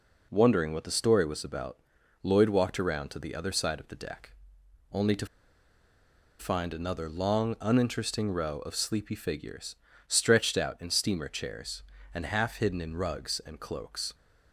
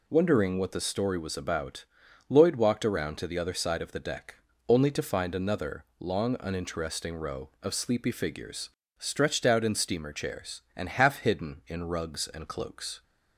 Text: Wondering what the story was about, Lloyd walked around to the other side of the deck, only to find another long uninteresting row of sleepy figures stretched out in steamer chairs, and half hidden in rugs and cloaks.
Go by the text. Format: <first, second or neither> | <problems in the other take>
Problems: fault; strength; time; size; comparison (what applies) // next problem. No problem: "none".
second | pauses between "to" and "find"; at 5.2 s; 1.1 s long // pauses between "figures" and "stretched"; slight; at 9.7 s; 0.32 s long; slight in the second